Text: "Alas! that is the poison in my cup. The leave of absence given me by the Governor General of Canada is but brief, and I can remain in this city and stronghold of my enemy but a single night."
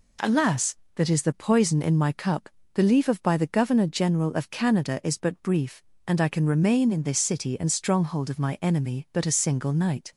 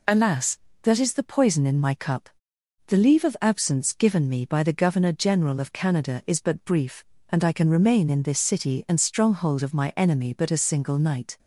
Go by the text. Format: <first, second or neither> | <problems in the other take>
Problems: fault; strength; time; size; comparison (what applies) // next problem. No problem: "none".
second | skips "absence given me"; at 3.2 s